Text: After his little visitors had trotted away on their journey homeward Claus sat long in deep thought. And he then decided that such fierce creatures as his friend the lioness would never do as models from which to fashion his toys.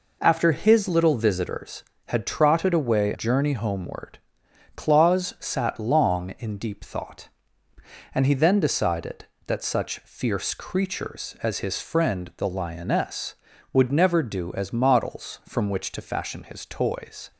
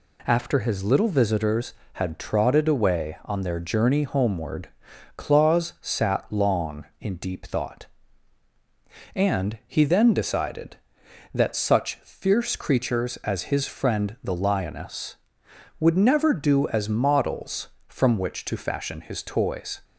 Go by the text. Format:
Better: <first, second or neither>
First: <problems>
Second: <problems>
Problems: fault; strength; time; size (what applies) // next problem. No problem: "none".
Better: second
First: skips "on their"; at 3.1 s // pauses between "homeward" and "Claus"; noticeable; at 4.1 s; 0.56 s long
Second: pauses between "homeward" and "Claus"; noticeable; at 4.6 s; 0.48 s long